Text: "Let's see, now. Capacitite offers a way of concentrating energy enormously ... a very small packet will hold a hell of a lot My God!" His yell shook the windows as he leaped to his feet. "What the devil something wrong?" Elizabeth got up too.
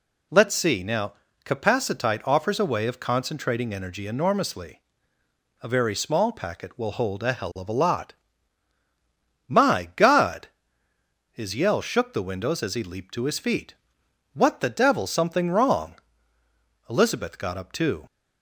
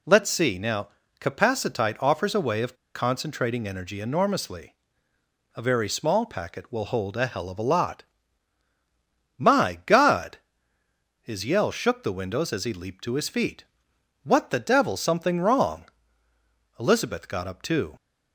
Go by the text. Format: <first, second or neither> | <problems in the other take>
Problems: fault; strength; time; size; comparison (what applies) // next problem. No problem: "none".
first | pauses between "of" and "concentrating"; slight; at 2.7 s; 0.20 s long // pauses between "lot" and "My"; strong; at 8.0 s; 1.3 s long; strong in the first